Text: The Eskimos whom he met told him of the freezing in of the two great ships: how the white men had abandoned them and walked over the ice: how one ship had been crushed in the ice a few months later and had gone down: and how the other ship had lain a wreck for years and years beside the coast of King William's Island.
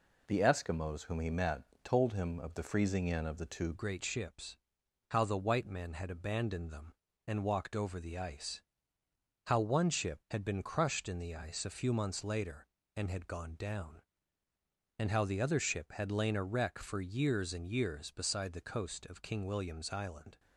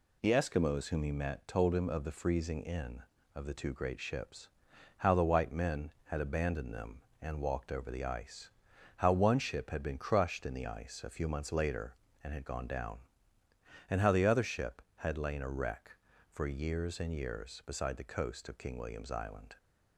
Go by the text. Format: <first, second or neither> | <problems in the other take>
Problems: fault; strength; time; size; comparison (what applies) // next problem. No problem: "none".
second | pauses between "met" and "told"; slight; at 1.6 s; 0.20 s long // changes voice at "great"; from 3.7 s on; 16.6 s long